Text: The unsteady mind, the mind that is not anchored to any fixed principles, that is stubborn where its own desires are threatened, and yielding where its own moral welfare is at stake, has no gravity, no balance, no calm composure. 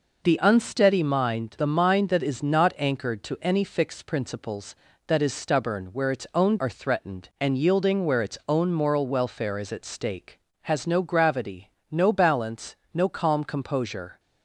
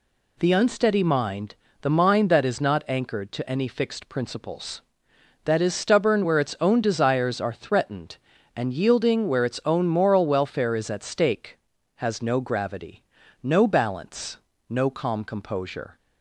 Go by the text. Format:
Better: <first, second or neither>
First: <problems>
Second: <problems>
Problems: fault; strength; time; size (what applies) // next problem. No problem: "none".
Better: second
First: skips "desires"; at 6.5 s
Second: none